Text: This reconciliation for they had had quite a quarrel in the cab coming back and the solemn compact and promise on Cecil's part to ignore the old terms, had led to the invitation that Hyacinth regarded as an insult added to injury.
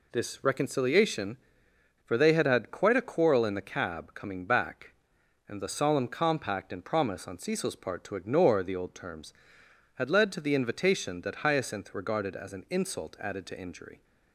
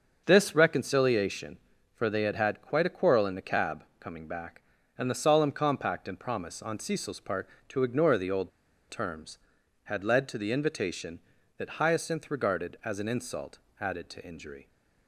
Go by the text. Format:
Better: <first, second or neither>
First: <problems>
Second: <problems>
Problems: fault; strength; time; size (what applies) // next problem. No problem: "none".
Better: first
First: none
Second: starts louder than the rest; until 1.2 s; 6.5 dB // pauses between "cab" and "coming"; slight; at 3.8 s; 0.16 s long // pauses between "old" and "terms"; at 8.5 s; 0.39 s long // pauses between "insult" and "added"; slight; at 13.5 s; 0.22 s long